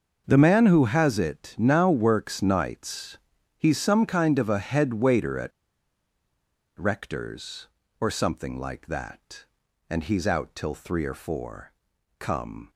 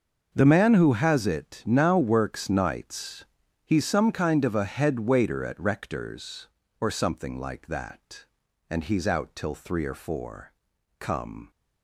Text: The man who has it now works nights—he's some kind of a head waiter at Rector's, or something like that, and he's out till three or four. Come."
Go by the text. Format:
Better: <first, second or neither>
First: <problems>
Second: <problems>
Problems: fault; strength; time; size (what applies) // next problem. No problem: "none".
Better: second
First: starts louder than the rest; until 1.2 s; 6.5 dB // pauses between "at" and "Rector's"; strong; at 5.5 s; 1.2 s long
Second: starts louder than the rest; until 1.3 s; 6.5 dB